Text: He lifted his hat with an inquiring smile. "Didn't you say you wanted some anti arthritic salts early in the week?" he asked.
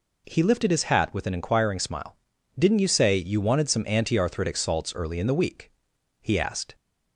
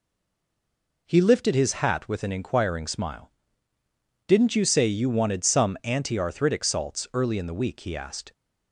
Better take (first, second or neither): first